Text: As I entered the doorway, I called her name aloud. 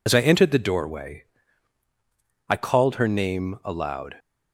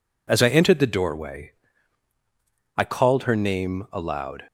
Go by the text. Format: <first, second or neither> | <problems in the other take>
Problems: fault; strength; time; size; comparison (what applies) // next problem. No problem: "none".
second | loses the start of "As"; at 0.0 s; 65 ms